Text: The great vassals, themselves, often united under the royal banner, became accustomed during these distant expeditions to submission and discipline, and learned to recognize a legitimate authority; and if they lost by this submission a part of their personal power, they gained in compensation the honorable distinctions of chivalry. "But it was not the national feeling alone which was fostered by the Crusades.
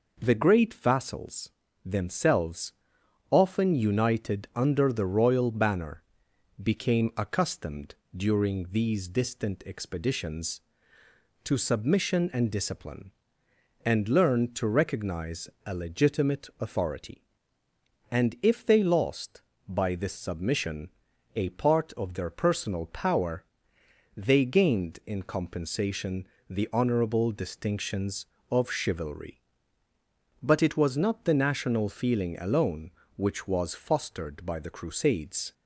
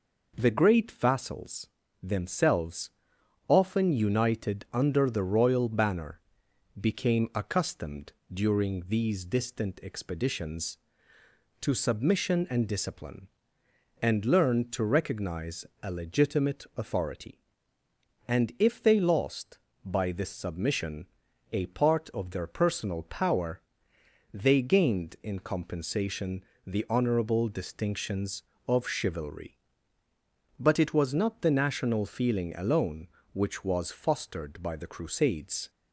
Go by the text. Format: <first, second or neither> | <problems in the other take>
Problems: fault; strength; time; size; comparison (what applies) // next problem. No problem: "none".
neither | pauses between "accustomed" and "during"; slight; the same in both // pauses between "recognize" and "a"; slight; the same in both // pauses between "submission" and "a"; noticeable; the same in both // pauses between "compensation" and "the"; slight; the same in both